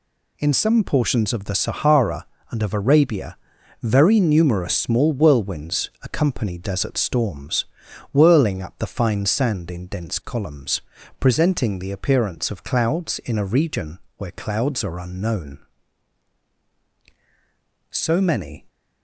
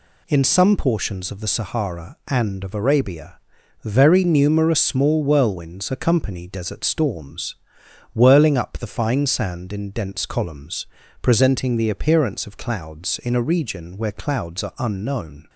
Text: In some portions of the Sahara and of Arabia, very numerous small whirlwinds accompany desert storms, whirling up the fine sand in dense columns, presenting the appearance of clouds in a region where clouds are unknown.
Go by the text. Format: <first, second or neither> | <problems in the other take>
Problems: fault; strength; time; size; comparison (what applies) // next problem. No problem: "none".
second | pauses between "region" and "where"; slight; at 13.9 s; 0.20 s long // goes on to say "So many"; noticeable; from 17.8 s on; 0.78 s long